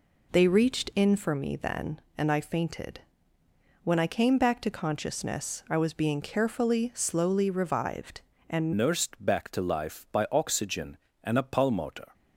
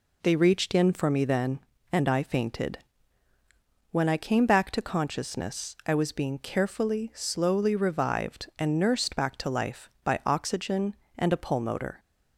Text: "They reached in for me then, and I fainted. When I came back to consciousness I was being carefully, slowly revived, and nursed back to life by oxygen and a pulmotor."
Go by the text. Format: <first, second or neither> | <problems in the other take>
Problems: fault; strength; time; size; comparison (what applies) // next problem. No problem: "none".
second | changes voice at "nursed"; from 8.7 s on; 3.4 s long